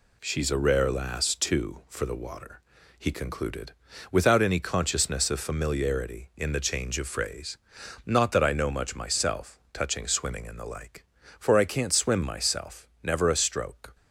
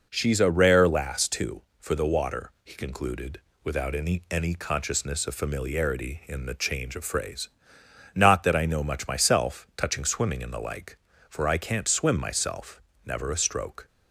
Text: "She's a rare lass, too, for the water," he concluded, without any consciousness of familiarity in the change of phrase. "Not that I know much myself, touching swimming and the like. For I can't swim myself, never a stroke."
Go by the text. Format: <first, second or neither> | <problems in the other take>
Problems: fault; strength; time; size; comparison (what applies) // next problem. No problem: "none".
first | says "any" twice; at 4.3 s